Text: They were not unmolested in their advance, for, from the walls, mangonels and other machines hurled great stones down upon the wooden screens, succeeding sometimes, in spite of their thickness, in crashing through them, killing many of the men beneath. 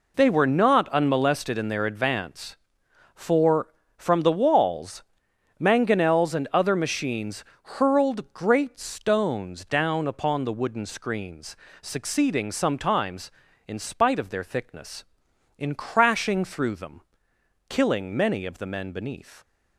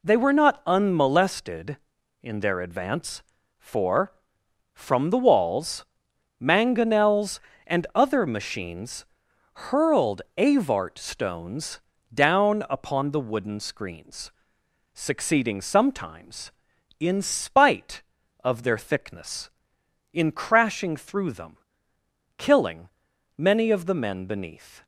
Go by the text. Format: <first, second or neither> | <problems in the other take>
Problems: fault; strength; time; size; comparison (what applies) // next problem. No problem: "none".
first | pauses between "machines" and "hurled"; noticeable; at 9.0 s; 0.50 s long; slight in the first // says "avart" for "great"; at 10.3 s // pauses between "stones" and "down"; slight; at 11.7 s; 0.34 s long // pauses between "killing" and "many"; noticeable; at 22.8 s; 0.48 s long